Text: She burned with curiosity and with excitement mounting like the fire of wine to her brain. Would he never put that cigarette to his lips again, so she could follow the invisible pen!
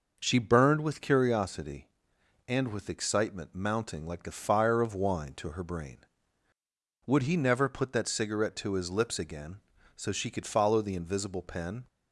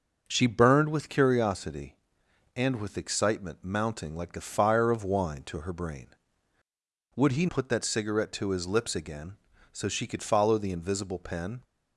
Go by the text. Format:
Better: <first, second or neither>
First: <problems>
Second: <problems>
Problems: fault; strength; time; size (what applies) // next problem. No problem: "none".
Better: first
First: none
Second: starts louder than the rest; noticeable; until 1.2 s; 6 dB // skips "never"; at 7.4 s